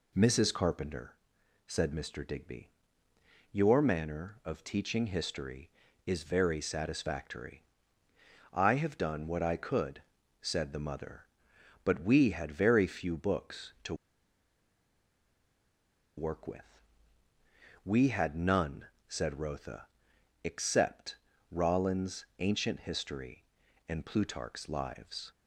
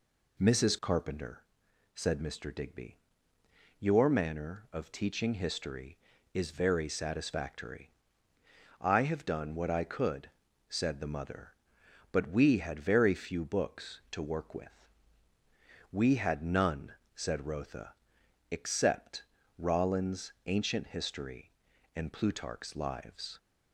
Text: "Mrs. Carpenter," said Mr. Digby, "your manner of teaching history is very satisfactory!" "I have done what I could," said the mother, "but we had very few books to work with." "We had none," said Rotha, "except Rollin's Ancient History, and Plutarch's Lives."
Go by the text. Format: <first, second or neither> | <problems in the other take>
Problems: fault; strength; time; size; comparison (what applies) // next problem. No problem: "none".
second | pauses between "to" and "work"; strong; at 13.9 s; 2.2 s long // pauses between "except" and "Rollin's"; at 21.1 s; 0.38 s long; also in the second // pauses between "Rollin's" and "Ancient"; slight; at 22.2 s; 0.16 s long; slight in the second